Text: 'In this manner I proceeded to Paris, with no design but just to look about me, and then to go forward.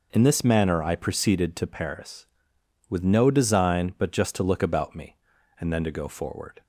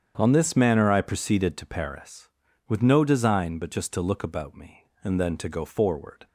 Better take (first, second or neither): first